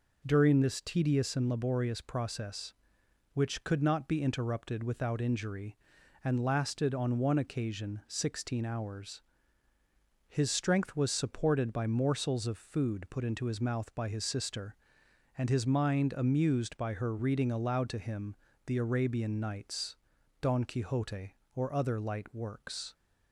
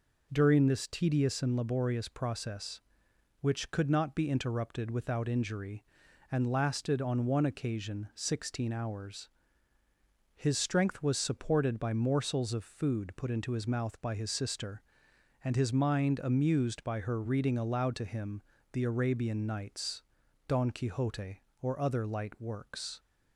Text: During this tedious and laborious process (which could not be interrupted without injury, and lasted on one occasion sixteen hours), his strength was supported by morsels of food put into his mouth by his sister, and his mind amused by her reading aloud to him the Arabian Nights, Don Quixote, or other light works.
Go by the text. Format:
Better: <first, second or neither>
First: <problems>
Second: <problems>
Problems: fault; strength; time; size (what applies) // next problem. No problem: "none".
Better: neither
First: pauses between "him" and "the"; slight; at 18.3 s; 0.30 s long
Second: pauses between "him" and "the"; slight; at 18.4 s; 0.30 s long